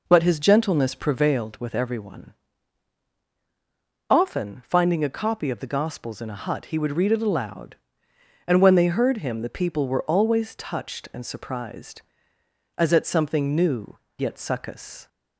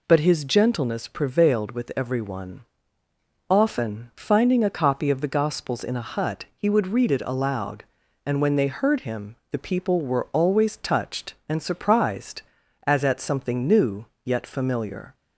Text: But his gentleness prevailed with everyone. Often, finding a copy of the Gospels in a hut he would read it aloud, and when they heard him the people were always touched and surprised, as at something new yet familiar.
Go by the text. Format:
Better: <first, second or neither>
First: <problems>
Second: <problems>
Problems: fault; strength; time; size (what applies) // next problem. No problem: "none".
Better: second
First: pauses between "new" and "yet"; slight; at 13.9 s; 0.18 s long // says "succous" for "familiar"; at 14.3 s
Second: pauses between "new" and "yet"; slight; at 14.0 s; 0.22 s long